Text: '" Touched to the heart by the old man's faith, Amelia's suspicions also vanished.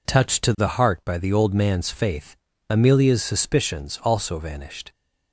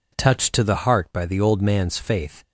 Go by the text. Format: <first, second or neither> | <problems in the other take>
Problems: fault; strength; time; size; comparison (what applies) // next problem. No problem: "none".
first | stops before "Amelia's suspicions also vanished"; at 2.4 s